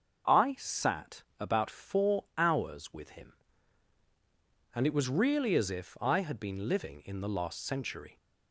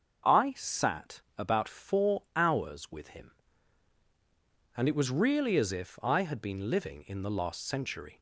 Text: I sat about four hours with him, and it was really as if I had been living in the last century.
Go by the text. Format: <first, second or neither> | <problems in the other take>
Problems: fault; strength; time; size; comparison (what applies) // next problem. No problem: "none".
neither | starts louder than the rest; the same in both // pauses between "sat" and "about"; slight; the same in both